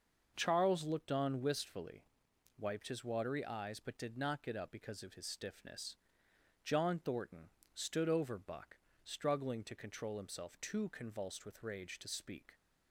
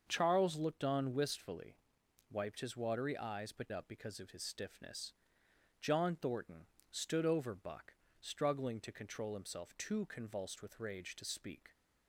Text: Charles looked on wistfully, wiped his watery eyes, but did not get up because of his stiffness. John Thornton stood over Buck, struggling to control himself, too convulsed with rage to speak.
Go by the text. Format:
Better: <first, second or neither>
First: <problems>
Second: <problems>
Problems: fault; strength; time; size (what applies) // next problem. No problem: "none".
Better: first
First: starts louder than the rest; until 1.3 s; 6 dB // pauses between "Thornton" and "stood"; slight; at 7.4 s; 0.24 s long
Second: starts louder than the rest; until 1.0 s; 6.5 dB // skips "did not get"; at 3.7 s // pauses between "Thornton" and "stood"; slight; at 6.6 s; 0.24 s long